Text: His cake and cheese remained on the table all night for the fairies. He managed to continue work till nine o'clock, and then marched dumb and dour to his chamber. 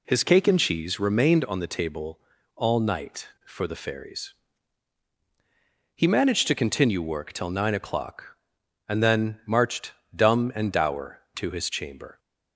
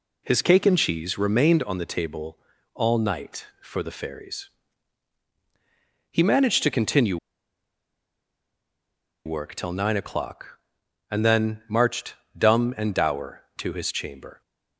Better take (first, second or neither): first